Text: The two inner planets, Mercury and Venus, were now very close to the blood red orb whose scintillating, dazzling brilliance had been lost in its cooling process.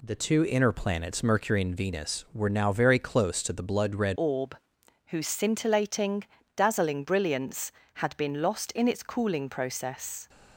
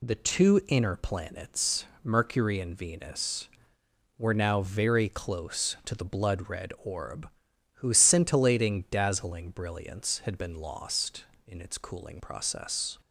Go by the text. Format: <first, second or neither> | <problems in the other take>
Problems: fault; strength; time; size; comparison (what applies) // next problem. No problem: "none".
second | changes voice at "orb"; from 4.1 s on; 6.1 s long // pauses between "orb" and "whose"; noticeable; at 4.5 s; 0.50 s long; noticeable in the second